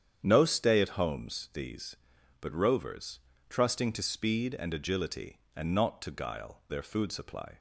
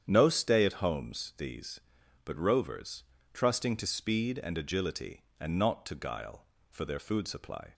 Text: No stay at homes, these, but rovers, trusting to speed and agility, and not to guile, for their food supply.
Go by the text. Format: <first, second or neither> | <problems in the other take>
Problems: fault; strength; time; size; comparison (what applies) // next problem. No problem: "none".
second | starts louder than the rest; strong; until 1.2 s; 9 dB; strong in the second // skips "for"; at 6.6 s